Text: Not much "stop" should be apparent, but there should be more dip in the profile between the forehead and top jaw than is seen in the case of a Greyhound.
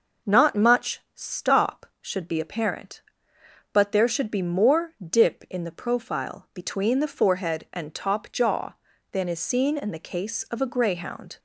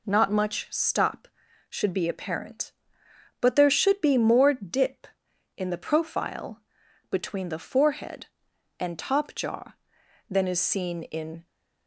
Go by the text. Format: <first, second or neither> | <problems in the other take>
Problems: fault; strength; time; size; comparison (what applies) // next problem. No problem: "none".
first | pauses between "profile" and "between"; noticeable; at 6.5 s; 0.50 s long // stops before "the case of a Greyhound"; at 11.4 s